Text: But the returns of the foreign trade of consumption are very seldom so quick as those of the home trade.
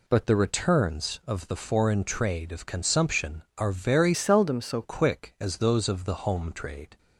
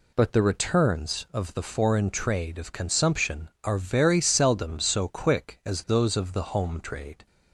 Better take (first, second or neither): second